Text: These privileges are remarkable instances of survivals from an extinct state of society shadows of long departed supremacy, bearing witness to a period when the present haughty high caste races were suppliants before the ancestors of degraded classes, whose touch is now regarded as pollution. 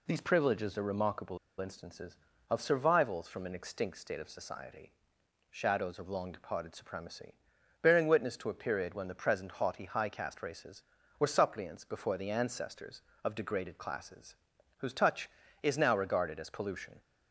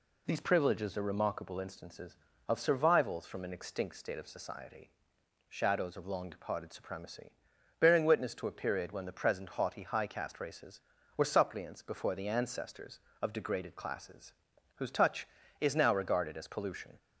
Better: second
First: pauses between "remarkable" and "instances"; slight; at 1.3 s; 0.23 s long // pauses between "society" and "shadows"; noticeable; at 4.9 s; 0.60 s long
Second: pauses between "society" and "shadows"; noticeable; at 4.8 s; 0.60 s long

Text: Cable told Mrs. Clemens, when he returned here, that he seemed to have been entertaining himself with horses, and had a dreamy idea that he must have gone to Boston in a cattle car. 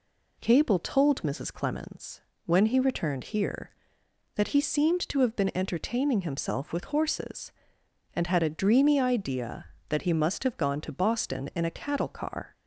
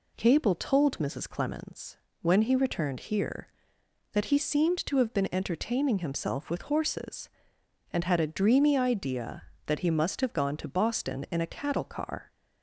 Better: neither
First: none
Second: none

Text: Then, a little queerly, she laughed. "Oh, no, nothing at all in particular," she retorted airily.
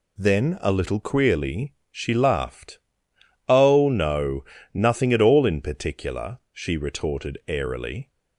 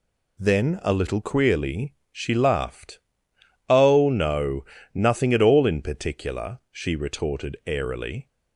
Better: neither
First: none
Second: none

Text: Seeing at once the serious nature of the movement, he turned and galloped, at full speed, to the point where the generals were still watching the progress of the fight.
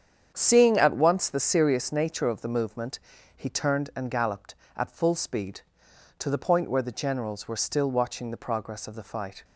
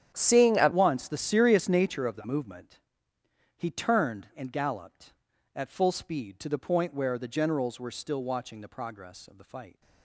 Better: first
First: starts louder than the rest; strong; until 1.3 s; 8 dB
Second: starts louder than the rest; strong; until 1.1 s; 9 dB // changes voice at "once"; from 0.7 s on; 9.1 s long

